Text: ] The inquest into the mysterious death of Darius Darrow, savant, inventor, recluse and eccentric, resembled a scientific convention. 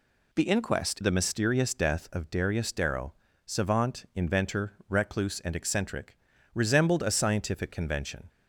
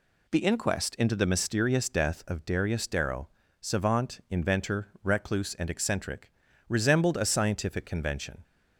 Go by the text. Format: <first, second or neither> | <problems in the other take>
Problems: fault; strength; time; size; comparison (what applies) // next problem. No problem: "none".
second | skips "into"; at 0.9 s